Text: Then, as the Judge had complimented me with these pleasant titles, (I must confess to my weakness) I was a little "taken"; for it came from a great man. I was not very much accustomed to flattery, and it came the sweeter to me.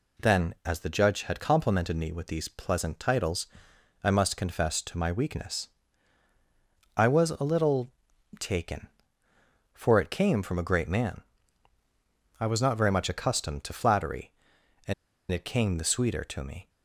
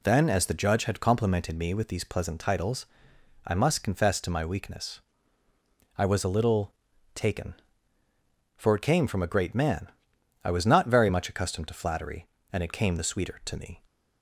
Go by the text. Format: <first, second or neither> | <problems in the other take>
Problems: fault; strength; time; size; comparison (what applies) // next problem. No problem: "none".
second | pauses between "little" and "taken"; noticeable; at 7.9 s; 0.48 s long; also in the second // pauses between "and" and "it"; at 14.9 s; 0.38 s long